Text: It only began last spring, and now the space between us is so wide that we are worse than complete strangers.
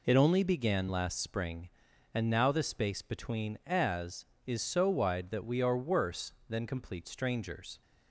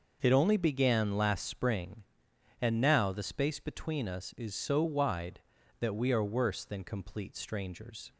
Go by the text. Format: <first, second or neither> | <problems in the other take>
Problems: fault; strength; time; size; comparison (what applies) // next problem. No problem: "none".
second | says "as" for "us"; at 3.6 s